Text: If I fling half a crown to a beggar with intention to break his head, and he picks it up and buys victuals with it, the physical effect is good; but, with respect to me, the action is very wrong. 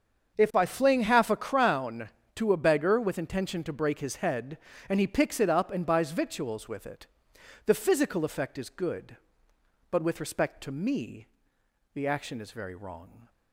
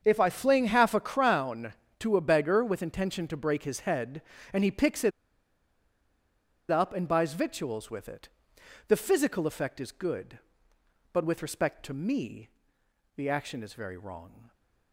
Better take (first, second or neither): first